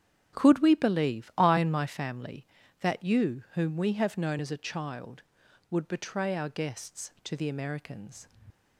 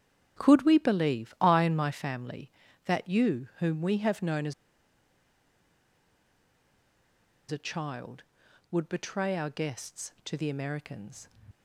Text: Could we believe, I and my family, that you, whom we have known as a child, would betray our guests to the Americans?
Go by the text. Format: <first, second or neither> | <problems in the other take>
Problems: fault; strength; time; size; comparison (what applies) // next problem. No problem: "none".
first | starts louder than the rest; strong; until 1.4 s; 9.5 dB; strong in the first // pauses between "as" and "a"; strong; at 4.5 s; 2.9 s long